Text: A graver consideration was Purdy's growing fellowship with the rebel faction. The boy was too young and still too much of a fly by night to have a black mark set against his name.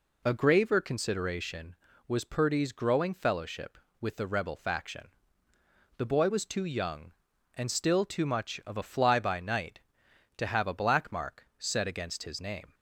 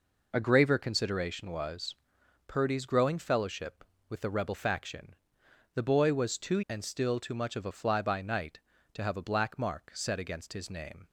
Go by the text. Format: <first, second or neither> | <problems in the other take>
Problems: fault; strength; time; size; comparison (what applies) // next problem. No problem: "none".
first | pauses between "was" and "Purdy's"; noticeable; at 1.9 s; 0.50 s long // skips "young"; at 6.6 s